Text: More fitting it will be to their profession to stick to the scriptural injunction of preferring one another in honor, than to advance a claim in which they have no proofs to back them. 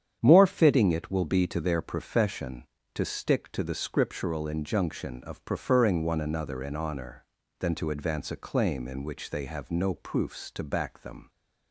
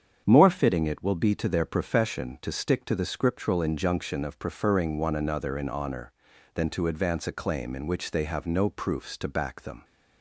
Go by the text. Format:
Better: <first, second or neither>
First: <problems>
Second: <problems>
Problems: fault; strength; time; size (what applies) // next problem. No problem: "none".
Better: neither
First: starts louder than the rest; strong; until 1.2 s; 8.5 dB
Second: starts louder than the rest; strong; until 1.2 s; 8 dB